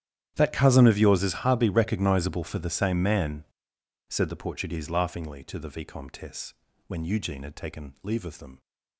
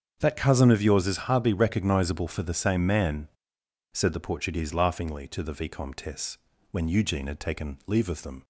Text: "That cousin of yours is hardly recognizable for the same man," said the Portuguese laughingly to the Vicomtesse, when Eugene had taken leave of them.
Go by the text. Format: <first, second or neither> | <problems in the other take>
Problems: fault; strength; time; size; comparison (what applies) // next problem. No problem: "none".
second | gets quieter; strong; throughout; 20 dB // starts louder than the rest; strong; until 1.3 s; 10.5 dB; strong in the second